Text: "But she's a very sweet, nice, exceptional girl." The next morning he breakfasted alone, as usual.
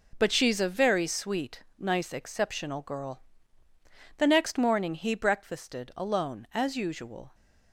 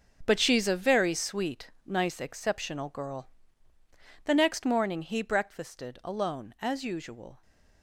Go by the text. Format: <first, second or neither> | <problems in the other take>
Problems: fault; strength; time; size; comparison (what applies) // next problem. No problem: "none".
first | gets quieter; strong; throughout; 10.5 dB